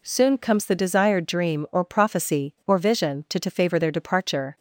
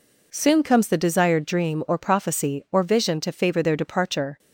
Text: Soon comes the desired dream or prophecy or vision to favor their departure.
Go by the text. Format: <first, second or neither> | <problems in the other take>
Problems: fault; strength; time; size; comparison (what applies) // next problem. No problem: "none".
second | says "to" twice; at 3.3 s